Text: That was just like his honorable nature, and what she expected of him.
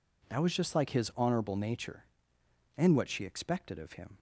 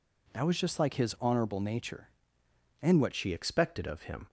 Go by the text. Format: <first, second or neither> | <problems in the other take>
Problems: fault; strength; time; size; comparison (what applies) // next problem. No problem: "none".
first | changes voice at "she"; from 3.1 s on; 1.1 s long